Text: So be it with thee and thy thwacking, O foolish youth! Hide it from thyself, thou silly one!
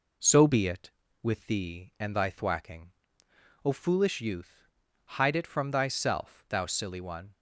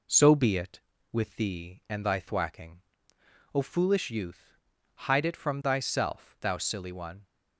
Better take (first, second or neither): neither